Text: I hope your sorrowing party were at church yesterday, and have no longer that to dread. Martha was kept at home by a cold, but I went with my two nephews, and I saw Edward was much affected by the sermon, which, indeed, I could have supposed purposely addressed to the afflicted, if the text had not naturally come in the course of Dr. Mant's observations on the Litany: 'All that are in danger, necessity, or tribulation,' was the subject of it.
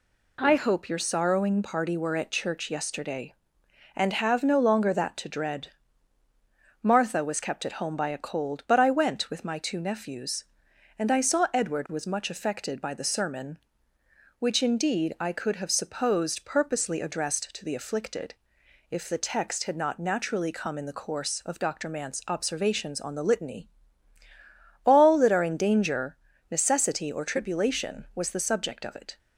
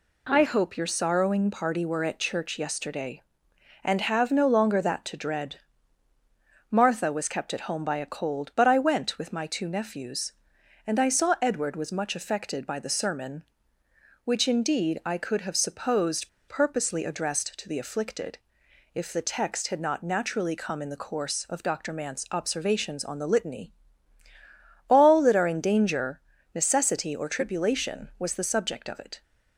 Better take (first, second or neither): first